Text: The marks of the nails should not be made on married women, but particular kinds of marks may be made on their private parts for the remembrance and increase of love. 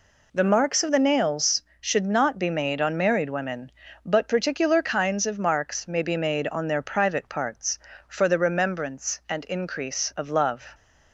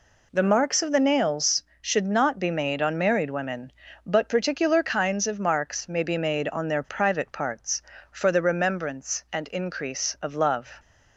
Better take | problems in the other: neither | none

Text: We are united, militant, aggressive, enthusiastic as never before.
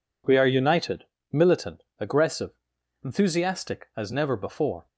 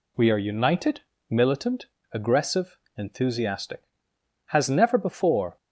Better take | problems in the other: first | says "has" for "as"; at 4.4 s

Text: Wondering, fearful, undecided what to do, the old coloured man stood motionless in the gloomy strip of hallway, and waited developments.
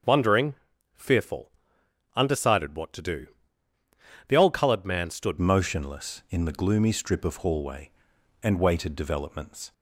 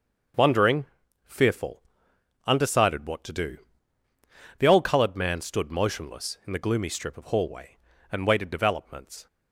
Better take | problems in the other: second | starts louder than the rest; until 1.4 s; 6.5 dB; also in the second // changes voice at "motionless"; from 5.3 s on; 4.4 s long

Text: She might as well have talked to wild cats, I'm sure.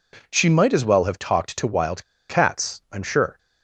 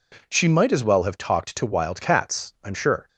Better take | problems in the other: second | pauses between "wild" and "cats"; slight; at 2.0 s; 0.26 s long

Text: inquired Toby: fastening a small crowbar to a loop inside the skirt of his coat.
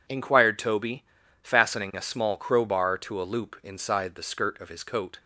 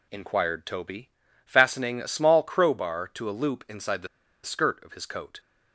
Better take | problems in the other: first | pauses between "the" and "skirt"; at 4.0 s; 0.36 s long

